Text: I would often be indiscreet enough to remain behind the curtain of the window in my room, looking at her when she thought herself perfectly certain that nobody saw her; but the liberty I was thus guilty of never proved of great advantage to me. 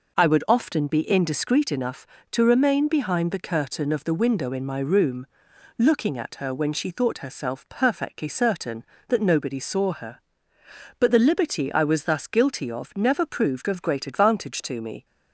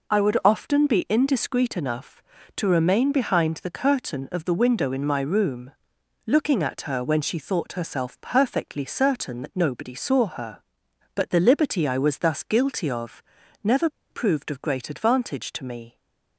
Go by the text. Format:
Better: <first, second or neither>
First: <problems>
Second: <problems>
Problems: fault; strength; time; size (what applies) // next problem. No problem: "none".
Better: first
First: none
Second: pauses between "of" and "never"; at 13.2 s; 0.42 s long // pauses between "never" and "proved"; slight; at 13.8 s; 0.22 s long